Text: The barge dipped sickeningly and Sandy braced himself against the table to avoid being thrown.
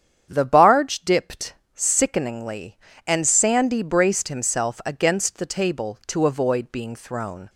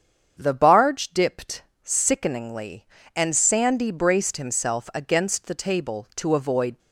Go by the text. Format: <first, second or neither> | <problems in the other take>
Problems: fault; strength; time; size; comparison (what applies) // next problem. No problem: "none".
first | starts louder than the rest; strong; until 1.4 s; 7.5 dB; strong in the first // pauses between "dipped" and "sickeningly"; slight; at 1.6 s; 0.18 s long; slight in the first // stops before "being thrown"; at 6.7 s